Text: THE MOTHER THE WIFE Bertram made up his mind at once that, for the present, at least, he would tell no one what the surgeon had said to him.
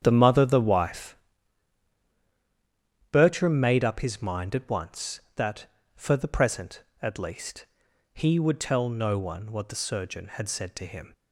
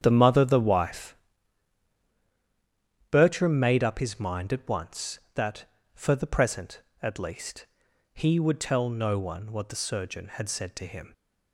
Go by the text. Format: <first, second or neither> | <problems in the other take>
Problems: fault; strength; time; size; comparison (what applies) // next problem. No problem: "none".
neither | starts louder than the rest; strong; the same in both // pauses between "WIFE" and "Bertram"; strong; the same in both